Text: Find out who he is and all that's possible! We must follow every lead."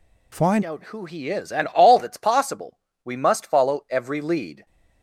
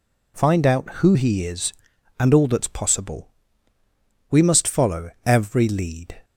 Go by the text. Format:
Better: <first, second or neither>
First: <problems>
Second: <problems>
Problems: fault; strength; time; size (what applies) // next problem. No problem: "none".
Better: second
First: changes voice at "out"; from 0.6 s on; 4.0 s long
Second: none